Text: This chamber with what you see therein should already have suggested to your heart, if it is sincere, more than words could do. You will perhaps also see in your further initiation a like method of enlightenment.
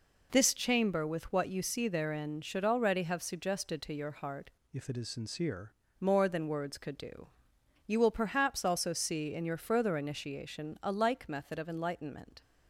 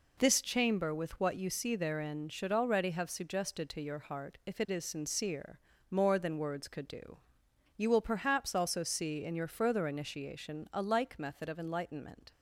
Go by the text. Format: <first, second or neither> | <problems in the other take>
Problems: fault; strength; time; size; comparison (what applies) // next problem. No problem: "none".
second | changes voice from "if" to "sincere"; from 4.7 to 5.7 s; 1.0 s long